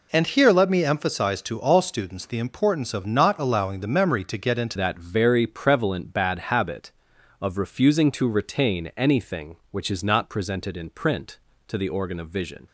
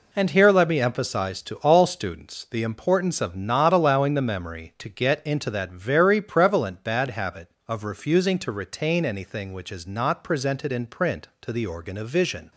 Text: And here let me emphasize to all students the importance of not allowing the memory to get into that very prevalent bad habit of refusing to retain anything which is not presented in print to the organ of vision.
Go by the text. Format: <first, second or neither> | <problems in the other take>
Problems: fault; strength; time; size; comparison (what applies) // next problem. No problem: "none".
second | changes voice at "that"; from 4.7 s on; 7.9 s long